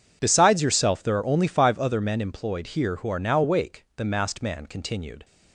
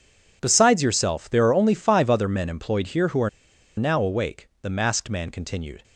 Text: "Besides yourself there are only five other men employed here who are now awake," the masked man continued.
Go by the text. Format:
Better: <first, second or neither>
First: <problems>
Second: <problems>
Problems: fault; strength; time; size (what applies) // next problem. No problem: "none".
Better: first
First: none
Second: pauses between "are" and "now"; noticeable; at 3.2 s; 0.49 s long